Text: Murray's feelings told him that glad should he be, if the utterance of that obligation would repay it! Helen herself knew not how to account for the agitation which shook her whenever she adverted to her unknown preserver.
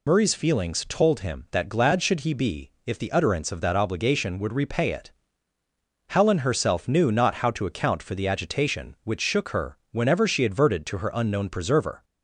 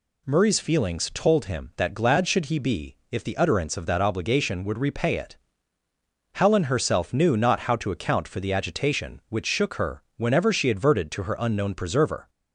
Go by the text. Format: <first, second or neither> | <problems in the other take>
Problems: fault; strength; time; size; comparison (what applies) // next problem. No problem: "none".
second | loses the start of "Murray's"; at 0.0 s; 65 ms